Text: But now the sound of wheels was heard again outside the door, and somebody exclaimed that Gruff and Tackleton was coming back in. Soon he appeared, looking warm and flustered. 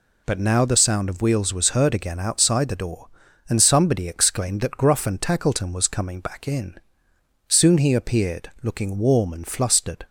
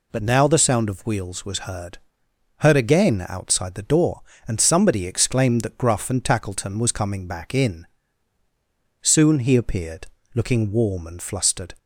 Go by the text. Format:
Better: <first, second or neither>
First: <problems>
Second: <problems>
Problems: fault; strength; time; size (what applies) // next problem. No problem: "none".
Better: first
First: none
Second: says "heard" twice; at 2.5 s